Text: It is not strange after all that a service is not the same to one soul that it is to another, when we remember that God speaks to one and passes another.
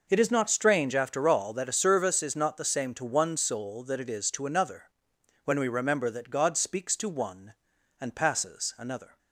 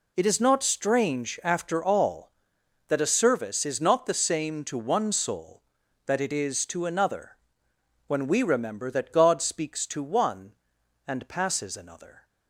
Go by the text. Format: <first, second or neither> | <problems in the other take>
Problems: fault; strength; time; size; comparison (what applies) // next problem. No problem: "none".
neither | none